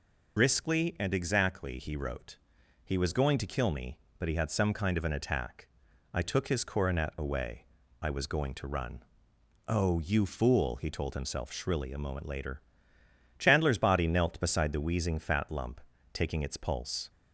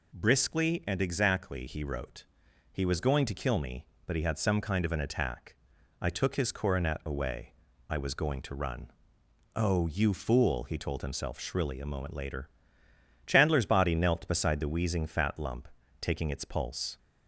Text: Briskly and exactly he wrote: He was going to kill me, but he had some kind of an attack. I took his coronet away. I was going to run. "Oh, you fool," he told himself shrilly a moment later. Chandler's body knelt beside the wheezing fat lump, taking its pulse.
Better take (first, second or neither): second